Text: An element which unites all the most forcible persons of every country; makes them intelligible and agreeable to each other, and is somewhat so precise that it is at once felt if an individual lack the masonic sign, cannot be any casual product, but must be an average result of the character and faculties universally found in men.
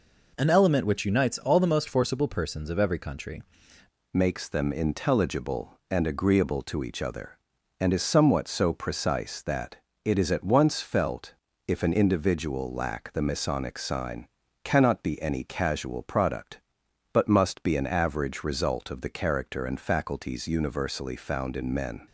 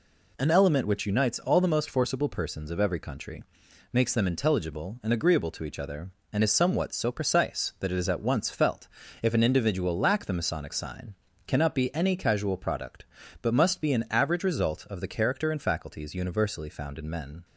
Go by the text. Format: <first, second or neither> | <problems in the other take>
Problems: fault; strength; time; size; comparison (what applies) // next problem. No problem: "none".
second | changes voice at "makes"; from 4.1 s on; 17.9 s long // pauses between "that" and "it"; slight; at 9.7 s; 0.26 s long // pauses between "felt" and "if"; slight; at 11.3 s; 0.32 s long; slight in the second